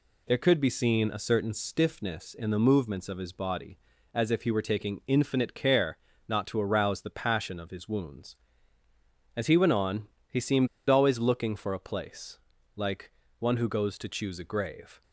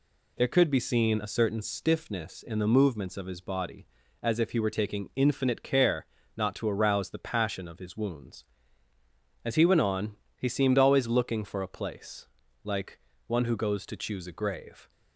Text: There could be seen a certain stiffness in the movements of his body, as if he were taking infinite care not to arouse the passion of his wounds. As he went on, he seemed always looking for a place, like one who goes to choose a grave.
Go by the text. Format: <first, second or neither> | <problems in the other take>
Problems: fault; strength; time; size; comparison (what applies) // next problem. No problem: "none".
second | pauses between "care" and "not"; slight; at 5.9 s; 0.32 s long; slight in the second // pauses between "seemed" and "always"; slight; at 10.6 s; 0.22 s long // pauses between "like" and "one"; slight; at 13.1 s; 0.26 s long; slight in the second